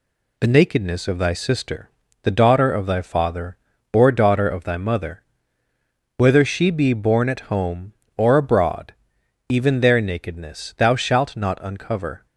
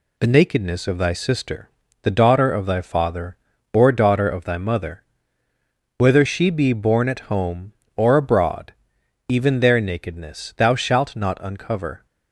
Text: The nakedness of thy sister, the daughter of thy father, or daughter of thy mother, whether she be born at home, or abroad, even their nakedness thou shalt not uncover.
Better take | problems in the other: neither | none

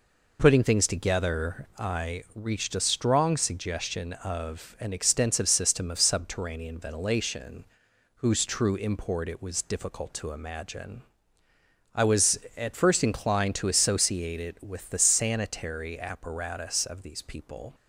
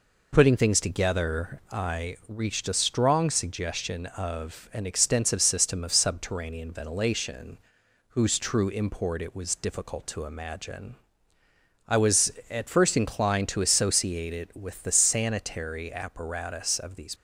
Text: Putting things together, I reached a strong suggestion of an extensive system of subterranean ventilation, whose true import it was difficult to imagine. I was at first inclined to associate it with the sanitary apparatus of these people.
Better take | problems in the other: first | stops before "people"; at 17.1 s

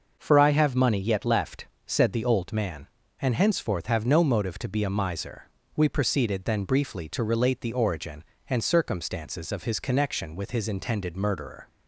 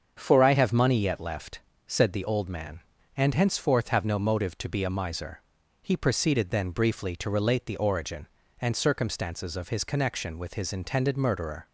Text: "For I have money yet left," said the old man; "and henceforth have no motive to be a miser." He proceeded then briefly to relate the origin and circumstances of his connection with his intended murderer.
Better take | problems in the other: second | starts louder than the rest; noticeable; until 1.2 s; 6 dB; strong in the second // says "We" for "He"; at 5.7 s

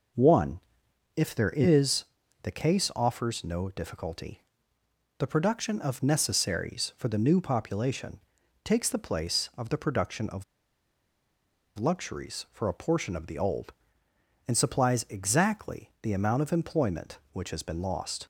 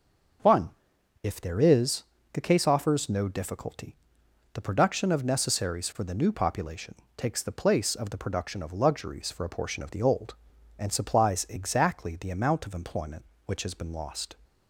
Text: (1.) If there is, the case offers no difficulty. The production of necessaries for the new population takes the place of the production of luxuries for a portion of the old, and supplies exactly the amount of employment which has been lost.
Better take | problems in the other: second | pauses between "population" and "takes"; at 8.1 s; 0.44 s long; slight in the second // pauses between "of" and "luxuries"; strong; at 10.4 s; 1.3 s long

